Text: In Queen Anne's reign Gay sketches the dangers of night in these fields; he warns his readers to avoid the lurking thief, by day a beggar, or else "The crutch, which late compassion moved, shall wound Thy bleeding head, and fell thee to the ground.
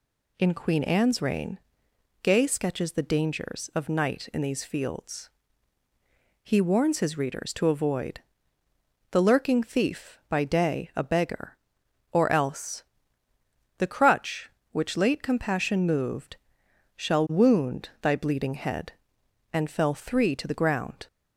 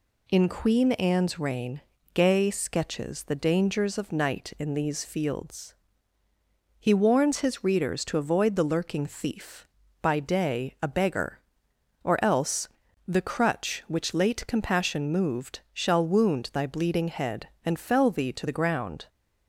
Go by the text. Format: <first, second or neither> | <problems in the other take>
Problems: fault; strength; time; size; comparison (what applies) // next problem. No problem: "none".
second | pauses between "reign" and "Gay"; noticeable; at 1.5 s; 0.64 s long; slight in the second // pauses between "avoid" and "the"; noticeable; at 8.1 s; 0.92 s long // pauses between "else" and "The"; noticeable; at 12.8 s; 0.94 s long; also in the second // says "three" for "thee"; at 19.9 s